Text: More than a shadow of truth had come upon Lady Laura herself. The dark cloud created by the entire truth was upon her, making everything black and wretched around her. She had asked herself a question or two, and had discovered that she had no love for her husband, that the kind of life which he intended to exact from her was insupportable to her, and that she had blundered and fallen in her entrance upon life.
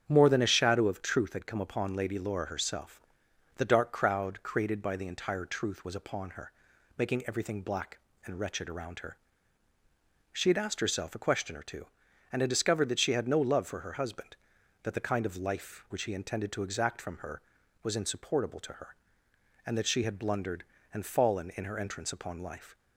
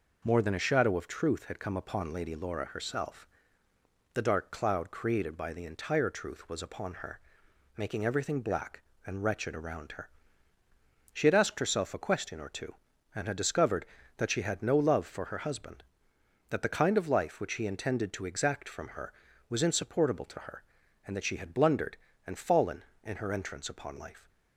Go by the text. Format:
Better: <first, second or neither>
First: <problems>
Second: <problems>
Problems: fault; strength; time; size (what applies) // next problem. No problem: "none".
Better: second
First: starts louder than the rest; strong; until 1.0 s; 8 dB // says "crowd" for "cloud"; at 3.9 s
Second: none